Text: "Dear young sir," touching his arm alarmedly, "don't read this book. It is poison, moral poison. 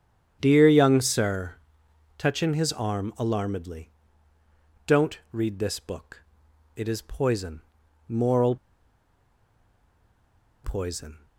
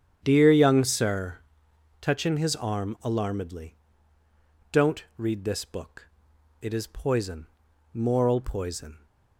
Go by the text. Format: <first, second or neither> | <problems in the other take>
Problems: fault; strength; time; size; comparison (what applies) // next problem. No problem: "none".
second | starts louder than the rest; strong; until 1.4 s; 9 dB; strong in the second // pauses between "moral" and "poison"; strong; at 8.5 s; 2.0 s long